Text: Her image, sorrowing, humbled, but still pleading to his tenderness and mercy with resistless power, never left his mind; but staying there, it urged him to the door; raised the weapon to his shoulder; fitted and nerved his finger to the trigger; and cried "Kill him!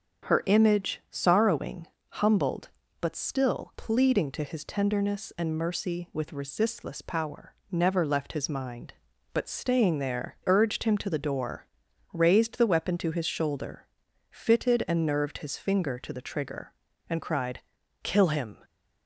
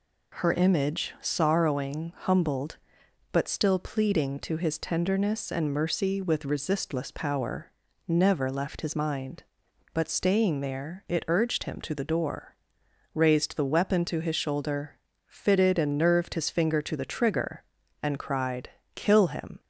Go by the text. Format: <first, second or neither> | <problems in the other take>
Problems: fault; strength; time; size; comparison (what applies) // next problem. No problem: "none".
second | starts louder than the rest; until 1.3 s; 6.5 dB // skips "it"; at 10.4 s // pauses between "cried" and "Kill"; at 17.5 s; 0.42 s long; slight in the second